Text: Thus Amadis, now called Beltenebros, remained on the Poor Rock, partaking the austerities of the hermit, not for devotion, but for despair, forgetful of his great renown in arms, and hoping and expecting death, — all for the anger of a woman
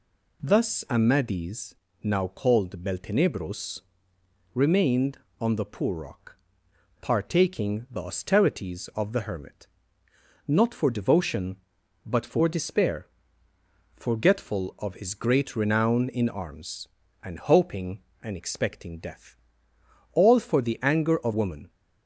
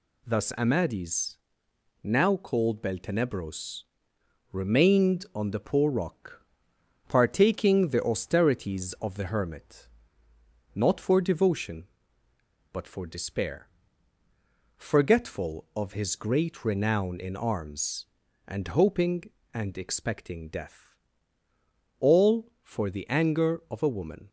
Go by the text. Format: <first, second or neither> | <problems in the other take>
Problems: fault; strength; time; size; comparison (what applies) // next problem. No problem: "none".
second | skips "a"; at 21.3 s